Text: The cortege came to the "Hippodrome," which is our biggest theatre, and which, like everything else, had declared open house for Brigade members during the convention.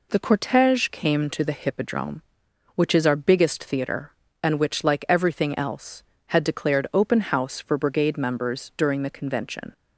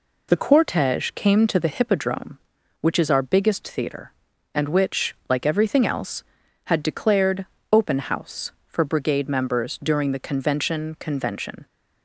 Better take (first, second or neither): first